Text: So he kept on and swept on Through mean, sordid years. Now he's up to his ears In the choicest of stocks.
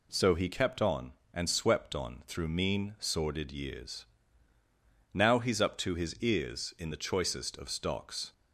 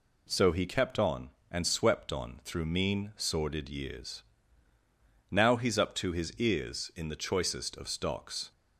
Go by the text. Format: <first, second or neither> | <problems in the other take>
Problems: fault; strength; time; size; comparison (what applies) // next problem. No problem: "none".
neither | none